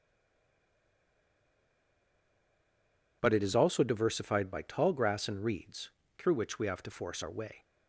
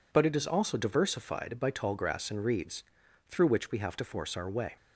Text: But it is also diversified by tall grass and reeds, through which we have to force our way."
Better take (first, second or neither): second